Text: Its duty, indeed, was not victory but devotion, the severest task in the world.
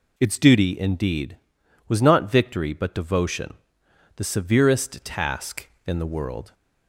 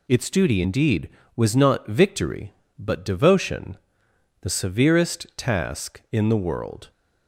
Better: neither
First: none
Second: none

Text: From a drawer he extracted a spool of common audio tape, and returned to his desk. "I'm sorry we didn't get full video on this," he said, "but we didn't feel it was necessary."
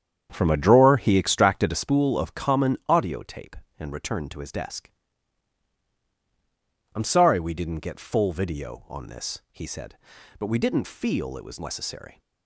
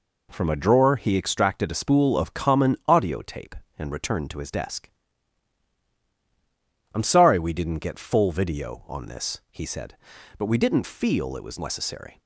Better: second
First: starts louder than the rest; strong; until 1.9 s; 8.5 dB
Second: none

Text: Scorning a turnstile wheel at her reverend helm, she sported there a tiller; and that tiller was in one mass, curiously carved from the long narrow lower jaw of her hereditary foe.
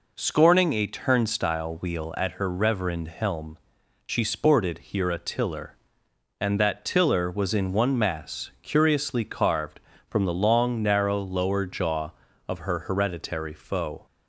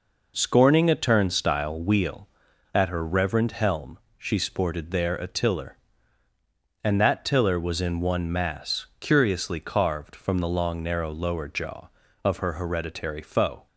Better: second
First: says "here" for "there"; at 4.7 s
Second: none

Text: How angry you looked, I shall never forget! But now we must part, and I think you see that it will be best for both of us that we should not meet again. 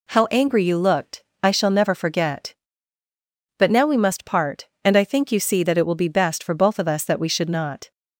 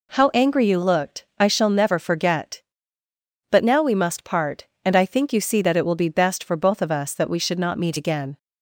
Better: second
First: stops before "meet again"; at 7.9 s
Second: none

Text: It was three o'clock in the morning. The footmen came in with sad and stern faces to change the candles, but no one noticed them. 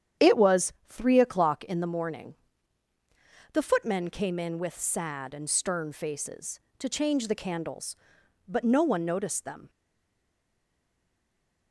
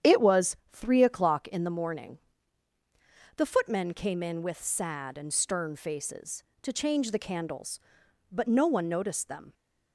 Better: second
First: starts louder than the rest; strong; until 1.3 s; 9 dB // pauses between "was" and "three"; slight; at 0.7 s; 0.18 s long // stays silent after the last word; noticeable; from 9.6 s on; 2.1 s long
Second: starts louder than the rest; strong; until 1.2 s; 9 dB // pauses between "was" and "three"; slight; at 0.5 s; 0.18 s long

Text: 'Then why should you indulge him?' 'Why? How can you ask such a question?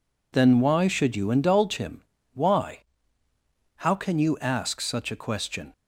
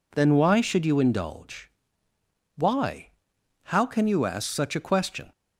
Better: first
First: none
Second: skips "him"; at 2.1 s

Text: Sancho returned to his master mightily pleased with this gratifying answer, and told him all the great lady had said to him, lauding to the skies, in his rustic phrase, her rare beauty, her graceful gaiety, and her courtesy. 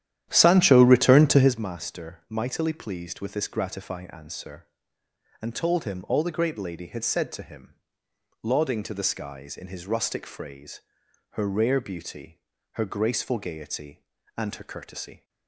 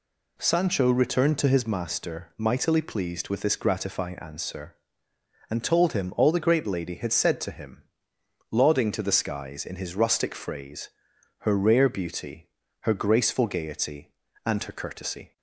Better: second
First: starts louder than the rest; strong; until 1.7 s; 11.5 dB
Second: none

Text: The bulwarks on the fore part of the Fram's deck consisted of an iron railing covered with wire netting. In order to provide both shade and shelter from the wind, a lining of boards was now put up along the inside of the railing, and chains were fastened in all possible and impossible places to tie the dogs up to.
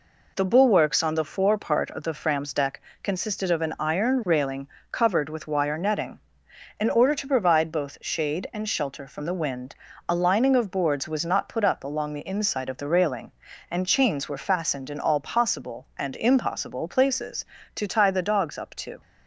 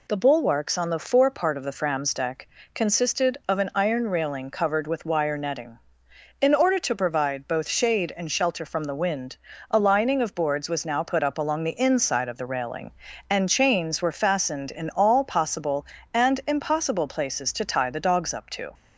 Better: second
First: pauses between "deck" and "consisted"; slight; at 2.7 s; 0.24 s long // pauses between "railing" and "covered"; slight; at 4.6 s; 0.22 s long // says "not" for "now"; at 11.2 s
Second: pauses between "deck" and "consisted"; slight; at 2.4 s; 0.30 s long

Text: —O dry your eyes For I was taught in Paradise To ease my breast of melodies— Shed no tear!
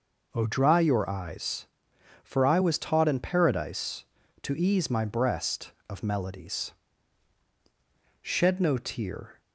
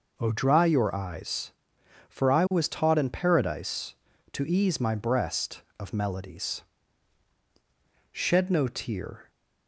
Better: neither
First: none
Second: none

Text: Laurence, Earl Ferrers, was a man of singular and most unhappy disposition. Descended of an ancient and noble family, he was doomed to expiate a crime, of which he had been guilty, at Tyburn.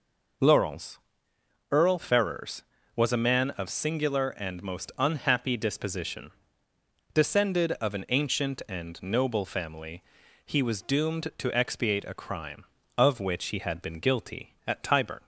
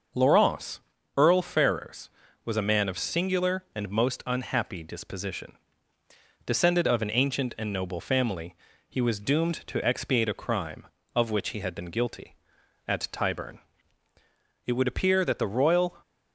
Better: first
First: none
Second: goes on to say "It would appear that the royal"; noticeable; from 14.6 s on; 1.3 s long

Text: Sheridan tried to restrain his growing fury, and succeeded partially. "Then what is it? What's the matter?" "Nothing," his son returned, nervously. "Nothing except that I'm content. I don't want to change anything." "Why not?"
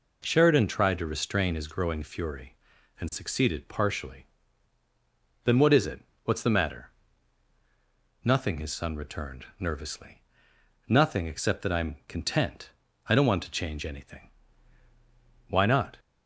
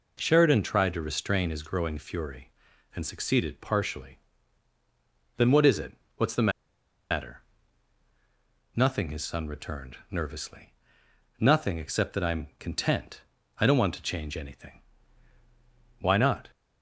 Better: first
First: none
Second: pauses between "the" and "matter"; noticeable; at 6.5 s; 0.60 s long

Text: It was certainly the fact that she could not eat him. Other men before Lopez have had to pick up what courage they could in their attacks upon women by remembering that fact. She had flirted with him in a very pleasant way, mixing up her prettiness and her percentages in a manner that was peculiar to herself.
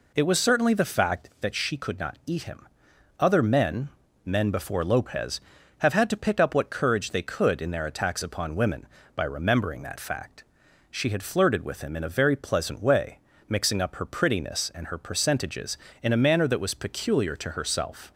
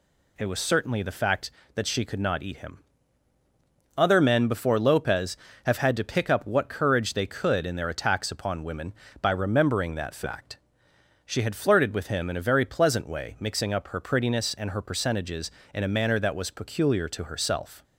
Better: second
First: says "men" twice; at 4.2 s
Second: none

